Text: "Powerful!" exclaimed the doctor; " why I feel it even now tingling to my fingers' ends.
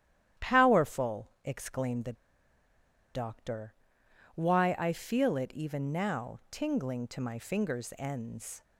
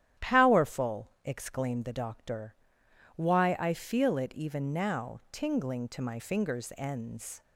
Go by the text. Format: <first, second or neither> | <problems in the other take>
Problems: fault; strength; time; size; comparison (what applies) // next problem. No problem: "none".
second | starts louder than the rest; strong; until 1.5 s; 10.5 dB; strong in the second // pauses between "the" and "doctor"; at 2.1 s; 1.0 s long